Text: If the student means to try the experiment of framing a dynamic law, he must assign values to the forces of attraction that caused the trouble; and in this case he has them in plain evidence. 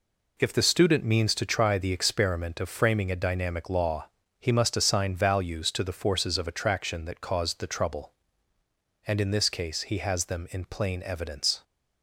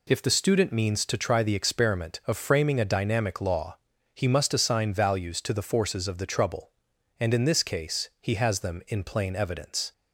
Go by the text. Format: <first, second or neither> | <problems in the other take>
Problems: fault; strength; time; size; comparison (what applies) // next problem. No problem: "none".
first | skips "attraction that caused"; at 6.1 s